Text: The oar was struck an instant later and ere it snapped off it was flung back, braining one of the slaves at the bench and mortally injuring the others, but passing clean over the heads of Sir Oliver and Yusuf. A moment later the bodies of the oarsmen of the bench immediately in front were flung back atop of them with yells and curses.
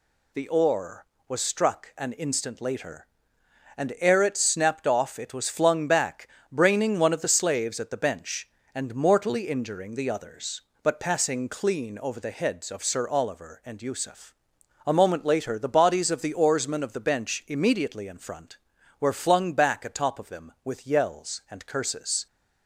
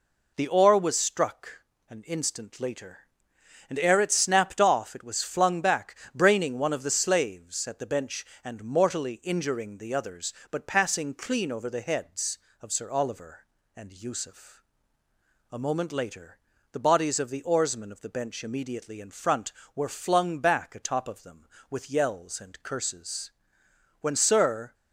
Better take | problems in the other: first | pauses between "struck" and "an"; slight; at 1.6 s; 0.28 s long // pauses between "later" and "the"; slight; at 16.3 s; 0.36 s long // goes on to say "When Sir"; noticeable; from 24.0 s on; 0.72 s long

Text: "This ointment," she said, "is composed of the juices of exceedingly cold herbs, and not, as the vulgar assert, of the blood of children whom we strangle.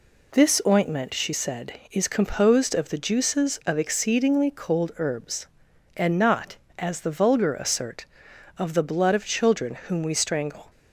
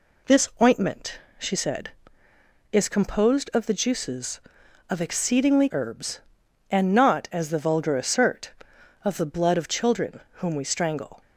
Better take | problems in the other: first | skips "cold"; at 5.6 s // pauses between "children" and "whom"; slight; at 10.2 s; 0.16 s long

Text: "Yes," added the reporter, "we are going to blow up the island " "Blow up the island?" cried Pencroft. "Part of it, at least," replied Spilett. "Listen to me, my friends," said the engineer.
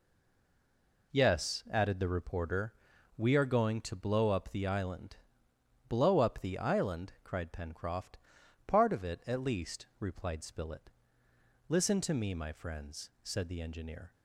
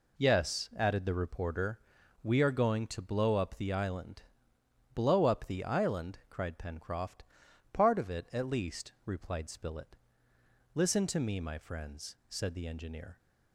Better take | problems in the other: second | stays silent before the first word; until 1.1 s; 1.1 s long

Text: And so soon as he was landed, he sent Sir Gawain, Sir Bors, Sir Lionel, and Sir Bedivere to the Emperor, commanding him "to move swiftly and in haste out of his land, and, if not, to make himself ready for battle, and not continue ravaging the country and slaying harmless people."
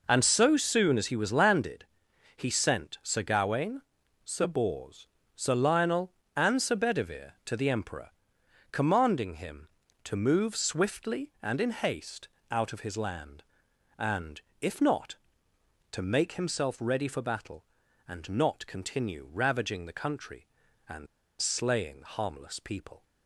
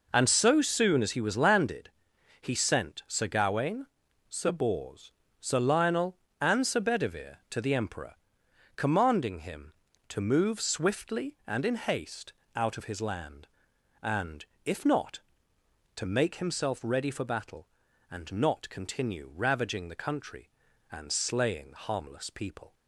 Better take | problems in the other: second | pauses between "haste" and "out"; slight; at 12.2 s; 0.24 s long; slight in the second // pauses between "and" and "slaying"; slight; at 21.0 s; 0.34 s long

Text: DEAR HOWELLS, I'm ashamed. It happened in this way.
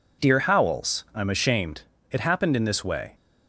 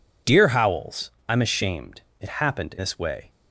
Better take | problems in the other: first | skips "in"; at 2.7 s

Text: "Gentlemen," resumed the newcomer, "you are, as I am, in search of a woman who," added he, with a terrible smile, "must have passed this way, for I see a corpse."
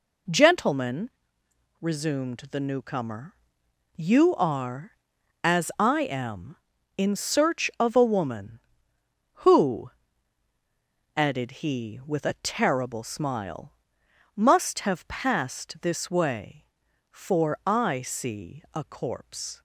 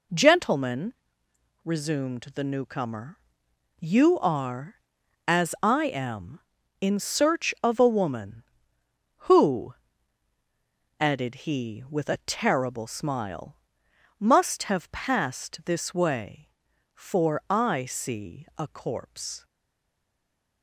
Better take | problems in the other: first | stays silent after the last word; noticeable; from 19.4 s on; 1.2 s long

